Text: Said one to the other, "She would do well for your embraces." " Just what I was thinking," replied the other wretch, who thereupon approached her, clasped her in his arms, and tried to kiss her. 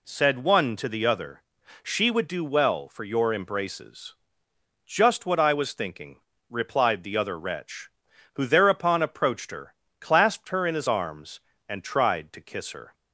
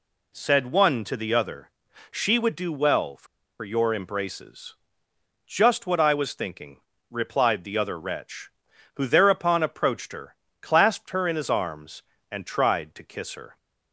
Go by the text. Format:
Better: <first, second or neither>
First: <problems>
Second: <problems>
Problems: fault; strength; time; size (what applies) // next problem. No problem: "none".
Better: first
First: none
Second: pauses between "for" and "your"; slight; at 3.2 s; 0.35 s long